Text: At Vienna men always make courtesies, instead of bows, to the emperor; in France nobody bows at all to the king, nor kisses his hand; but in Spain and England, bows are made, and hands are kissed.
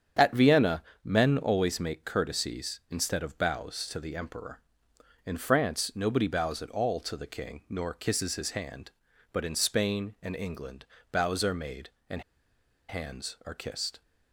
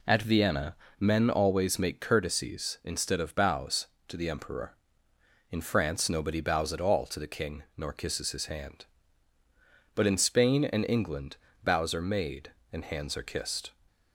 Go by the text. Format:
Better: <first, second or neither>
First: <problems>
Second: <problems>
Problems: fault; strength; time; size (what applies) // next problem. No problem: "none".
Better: second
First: starts louder than the rest; strong; until 1.4 s; 8 dB // pauses between "Vienna" and "men"; slight; at 0.8 s; 0.22 s long // pauses between "and" and "hands"; noticeable; at 12.2 s; 0.67 s long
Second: pauses between "Vienna" and "men"; slight; at 0.7 s; 0.24 s long